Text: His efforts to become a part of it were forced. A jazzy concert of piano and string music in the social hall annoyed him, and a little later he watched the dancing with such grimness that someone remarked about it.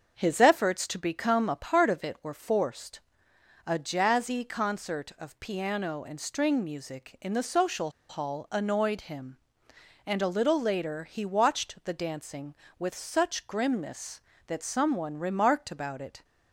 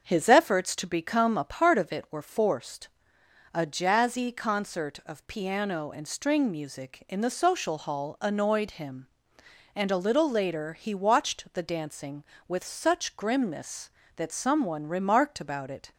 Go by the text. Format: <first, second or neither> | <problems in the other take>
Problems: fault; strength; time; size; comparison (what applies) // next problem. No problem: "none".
second | starts louder than the rest; until 1.1 s; 6.5 dB; also in the second // pauses between "social" and "hall"; slight; at 7.9 s; 0.19 s long